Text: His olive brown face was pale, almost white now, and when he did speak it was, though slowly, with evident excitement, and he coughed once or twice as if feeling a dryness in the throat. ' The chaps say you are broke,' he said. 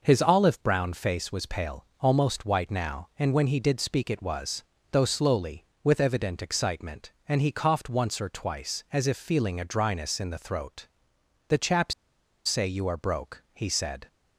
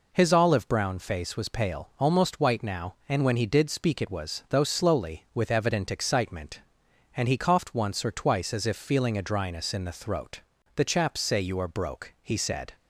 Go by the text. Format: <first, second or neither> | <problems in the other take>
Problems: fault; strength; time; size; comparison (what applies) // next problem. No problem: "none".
second | pauses between "chaps" and "say"; noticeable; at 11.9 s; 0.53 s long